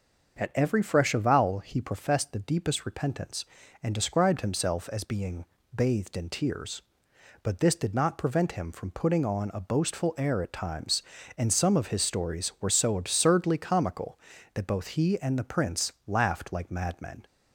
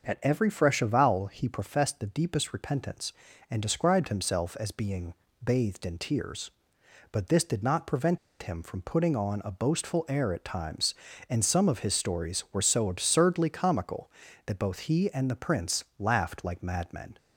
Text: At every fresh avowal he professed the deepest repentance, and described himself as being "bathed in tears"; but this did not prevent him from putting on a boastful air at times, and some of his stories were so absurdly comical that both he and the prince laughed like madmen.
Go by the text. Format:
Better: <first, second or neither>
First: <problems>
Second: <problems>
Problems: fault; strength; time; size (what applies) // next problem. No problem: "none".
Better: first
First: starts louder than the rest; until 1.4 s; 6.5 dB // pauses between "being" and "bathed"; slight; at 5.4 s; 0.28 s long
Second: starts louder than the rest; until 1.0 s; 6.5 dB // pauses between "being" and "bathed"; slight; at 5.1 s; 0.28 s long // pauses between "prevent" and "him"; slight; at 8.1 s; 0.24 s long